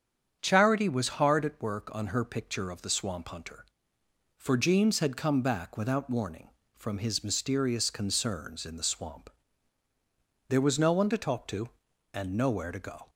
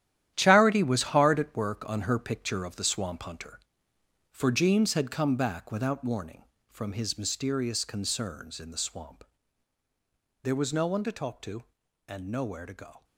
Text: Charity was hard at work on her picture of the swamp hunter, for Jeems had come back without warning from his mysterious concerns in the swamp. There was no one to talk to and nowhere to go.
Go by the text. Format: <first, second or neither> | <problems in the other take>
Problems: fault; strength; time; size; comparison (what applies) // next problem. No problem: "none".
first | gets quieter; strong; throughout; 10.5 dB // starts louder than the rest; strong; until 1.3 s; 11.5 dB; strong in the first